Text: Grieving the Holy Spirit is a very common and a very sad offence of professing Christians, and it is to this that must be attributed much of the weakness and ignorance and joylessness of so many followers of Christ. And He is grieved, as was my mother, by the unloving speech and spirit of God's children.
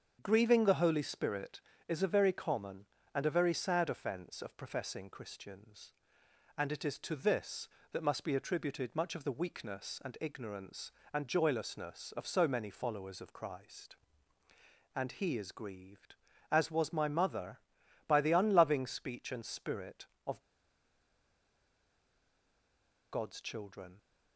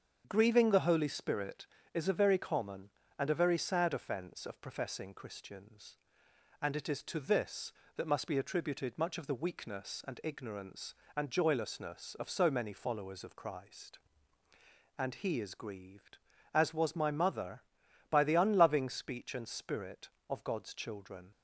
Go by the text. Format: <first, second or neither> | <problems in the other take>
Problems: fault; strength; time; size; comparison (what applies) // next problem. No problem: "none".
second | starts louder than the rest; until 1.2 s; 7 dB; strong in the second // pauses between "of" and "God's"; strong; at 20.4 s; 2.7 s long